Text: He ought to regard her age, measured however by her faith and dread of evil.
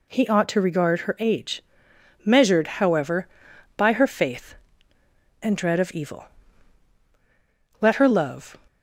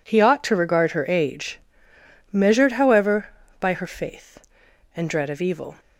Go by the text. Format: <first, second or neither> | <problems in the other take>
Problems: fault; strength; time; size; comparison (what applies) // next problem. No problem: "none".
second | goes on to say "Let her love"; noticeable; from 7.7 s on; 0.78 s long